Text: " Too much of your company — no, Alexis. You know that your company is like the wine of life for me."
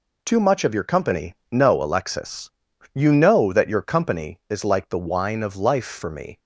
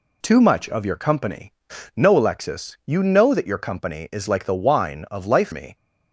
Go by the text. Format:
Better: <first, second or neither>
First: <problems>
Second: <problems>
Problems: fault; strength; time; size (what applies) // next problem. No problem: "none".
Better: first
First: none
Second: skips "for"; at 5.5 s